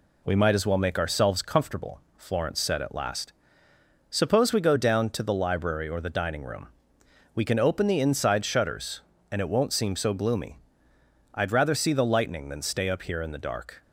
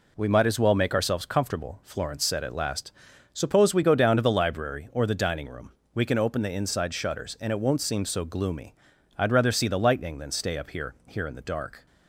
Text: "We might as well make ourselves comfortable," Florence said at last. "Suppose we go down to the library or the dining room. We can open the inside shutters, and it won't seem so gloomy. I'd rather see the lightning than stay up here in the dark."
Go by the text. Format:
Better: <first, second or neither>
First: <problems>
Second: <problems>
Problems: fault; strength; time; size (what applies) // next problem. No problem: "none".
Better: first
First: none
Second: says "here" twice; at 11.0 s